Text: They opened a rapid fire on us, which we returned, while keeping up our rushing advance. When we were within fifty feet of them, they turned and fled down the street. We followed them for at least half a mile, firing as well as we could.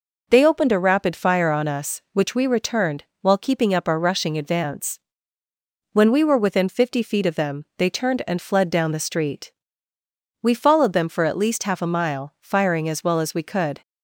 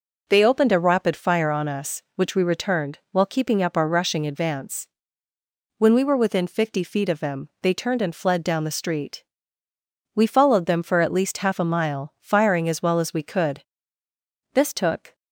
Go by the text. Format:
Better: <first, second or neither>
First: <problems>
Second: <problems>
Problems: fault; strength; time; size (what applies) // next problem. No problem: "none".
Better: first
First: none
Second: goes on to say "This took"; noticeable; from 14.5 s on; 0.62 s long